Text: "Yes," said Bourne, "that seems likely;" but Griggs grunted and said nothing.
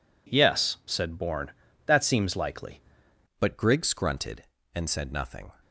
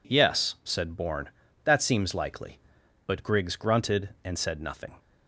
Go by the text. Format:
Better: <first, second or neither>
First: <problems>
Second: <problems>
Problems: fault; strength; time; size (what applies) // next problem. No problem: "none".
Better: second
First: changes voice at "but"; from 3.3 s on; 2.2 s long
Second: none